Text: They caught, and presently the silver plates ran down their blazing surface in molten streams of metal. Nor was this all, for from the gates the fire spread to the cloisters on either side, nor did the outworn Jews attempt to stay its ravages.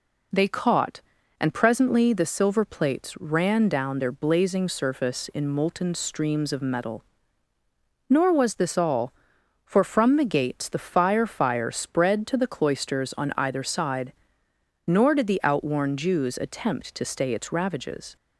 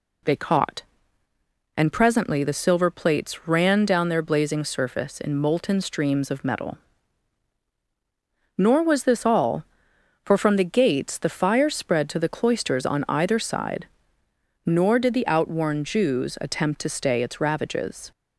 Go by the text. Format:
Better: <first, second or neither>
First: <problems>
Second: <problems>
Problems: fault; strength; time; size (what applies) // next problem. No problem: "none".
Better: second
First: says "fire" twice; at 11.2 s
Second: none